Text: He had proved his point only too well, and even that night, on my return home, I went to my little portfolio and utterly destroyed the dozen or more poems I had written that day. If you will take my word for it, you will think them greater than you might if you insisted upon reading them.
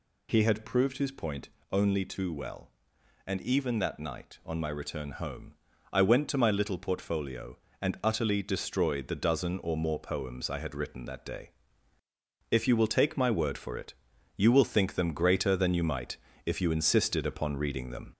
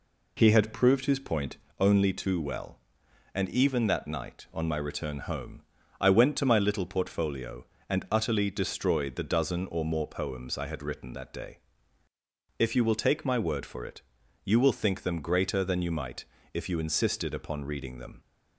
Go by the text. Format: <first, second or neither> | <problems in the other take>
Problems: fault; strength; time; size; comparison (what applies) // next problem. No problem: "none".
second | gets louder; slight; throughout; 3.5 dB // pauses between "point" and "only"; slight; at 1.4 s; 0.24 s long; slight in the second // pauses between "might" and "if"; slight; at 16.1 s; 0.30 s long; slight in the second